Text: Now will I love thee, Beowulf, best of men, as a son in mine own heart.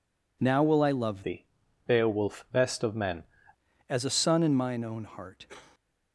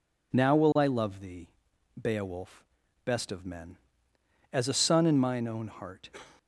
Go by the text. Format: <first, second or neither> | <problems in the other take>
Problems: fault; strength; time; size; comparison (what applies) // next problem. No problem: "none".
second | changes voice from "thee" to "men"; from 1.2 to 3.2 s; 2.0 s long